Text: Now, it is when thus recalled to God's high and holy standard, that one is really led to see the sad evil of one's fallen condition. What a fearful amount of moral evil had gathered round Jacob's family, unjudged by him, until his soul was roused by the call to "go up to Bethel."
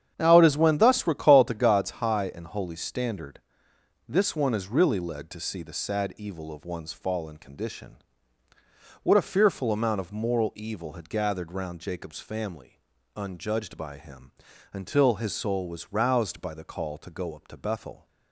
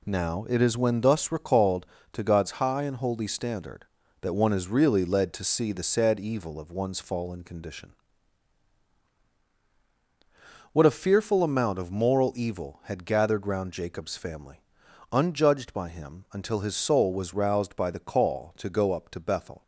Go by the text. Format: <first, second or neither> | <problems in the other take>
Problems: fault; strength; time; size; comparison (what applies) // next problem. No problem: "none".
second | starts louder than the rest; strong; until 1.1 s; 9 dB // says "this" for "that"; at 4.0 s